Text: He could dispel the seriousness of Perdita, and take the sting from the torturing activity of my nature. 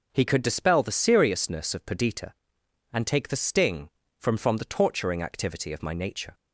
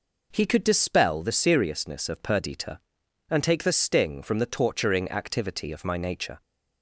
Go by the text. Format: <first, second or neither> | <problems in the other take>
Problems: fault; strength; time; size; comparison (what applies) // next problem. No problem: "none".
second | says "from" twice; at 4.3 s